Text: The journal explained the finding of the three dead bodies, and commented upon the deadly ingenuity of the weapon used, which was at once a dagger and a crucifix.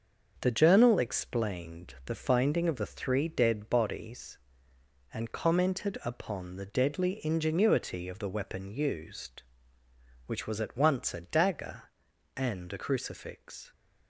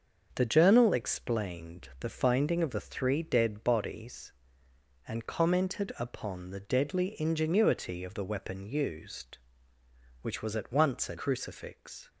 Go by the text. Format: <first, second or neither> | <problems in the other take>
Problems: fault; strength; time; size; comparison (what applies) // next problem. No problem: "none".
first | starts louder than the rest; until 1.3 s; 6.5 dB; also in the first // skips "dagger and a"; at 11.1 s